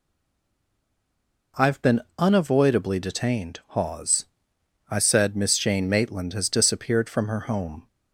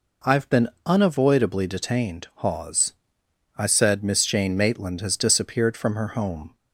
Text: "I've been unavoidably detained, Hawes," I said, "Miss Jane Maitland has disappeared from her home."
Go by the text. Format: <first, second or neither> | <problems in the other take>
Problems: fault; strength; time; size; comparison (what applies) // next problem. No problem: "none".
second | stays silent before the first word; noticeable; until 1.5 s; 1.5 s long // pauses between "been" and "unavoidably"; slight; at 2.0 s; 0.18 s long; slight in the second